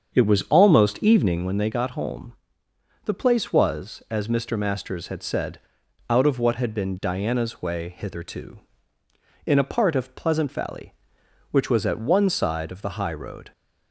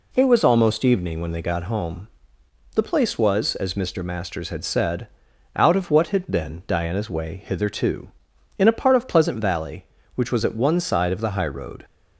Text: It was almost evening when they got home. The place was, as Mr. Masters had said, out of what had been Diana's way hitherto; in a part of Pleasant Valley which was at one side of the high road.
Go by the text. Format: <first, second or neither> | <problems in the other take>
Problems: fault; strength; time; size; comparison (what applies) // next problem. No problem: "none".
second | starts louder than the rest; strong; until 1.5 s; 7 dB